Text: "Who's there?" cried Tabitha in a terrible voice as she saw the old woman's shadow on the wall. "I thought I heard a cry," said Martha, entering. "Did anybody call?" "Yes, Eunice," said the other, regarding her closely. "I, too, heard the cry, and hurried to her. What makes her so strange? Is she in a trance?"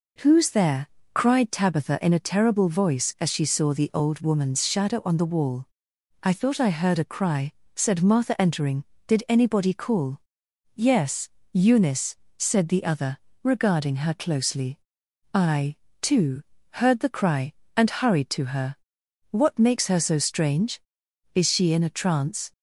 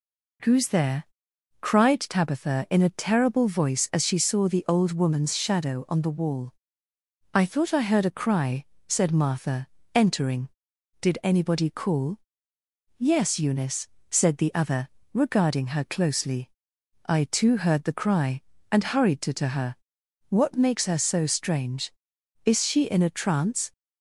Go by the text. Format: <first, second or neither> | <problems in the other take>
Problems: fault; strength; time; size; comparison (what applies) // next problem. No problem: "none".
first | says "to" twice; at 19.3 s